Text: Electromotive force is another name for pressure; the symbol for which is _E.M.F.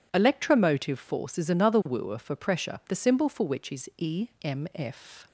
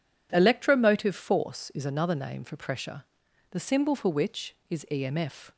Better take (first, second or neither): second